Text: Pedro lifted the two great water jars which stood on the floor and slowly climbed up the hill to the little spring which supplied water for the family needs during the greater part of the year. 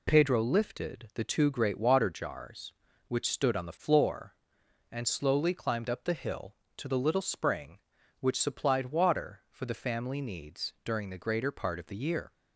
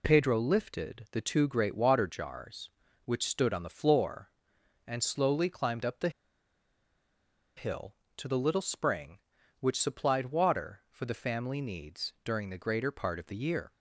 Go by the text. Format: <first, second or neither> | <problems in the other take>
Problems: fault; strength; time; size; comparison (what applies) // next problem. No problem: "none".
first | pauses between "the" and "hill"; strong; at 6.0 s; 1.4 s long